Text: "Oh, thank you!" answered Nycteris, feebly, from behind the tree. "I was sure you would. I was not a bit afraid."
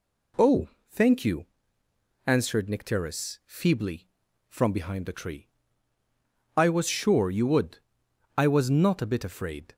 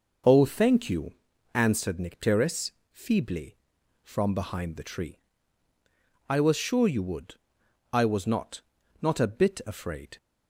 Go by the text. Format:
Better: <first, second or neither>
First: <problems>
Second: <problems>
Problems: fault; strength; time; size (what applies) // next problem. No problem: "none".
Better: first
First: none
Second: says "not" twice; at 9.0 s